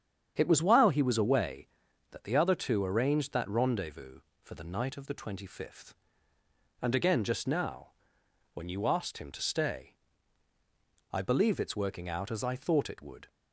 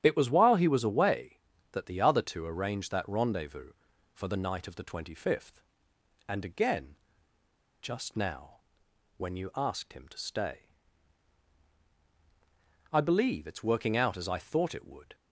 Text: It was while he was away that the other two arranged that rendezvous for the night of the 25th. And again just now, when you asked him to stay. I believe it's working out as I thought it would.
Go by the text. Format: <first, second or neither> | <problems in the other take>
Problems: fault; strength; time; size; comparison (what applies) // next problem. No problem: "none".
first | starts louder than the rest; strong; until 1.0 s; 9.5 dB; strong in the first // pauses between "again" and "just"; noticeable; at 6.9 s; 0.86 s long